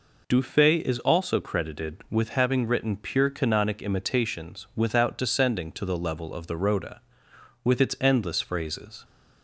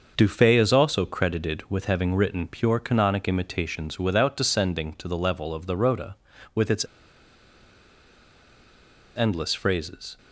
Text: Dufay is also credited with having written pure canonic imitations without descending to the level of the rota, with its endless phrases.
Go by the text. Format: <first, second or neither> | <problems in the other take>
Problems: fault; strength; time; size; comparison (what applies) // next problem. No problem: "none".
first | starts louder than the rest; until 1.1 s; 6 dB // pauses between "its" and "endless"; strong; at 6.8 s; 2.3 s long